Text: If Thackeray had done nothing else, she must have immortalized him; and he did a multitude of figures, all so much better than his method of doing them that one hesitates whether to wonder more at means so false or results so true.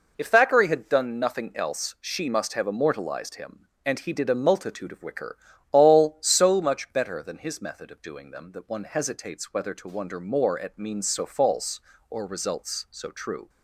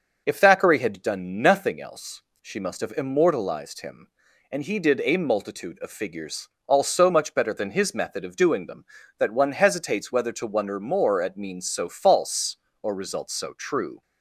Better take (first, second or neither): second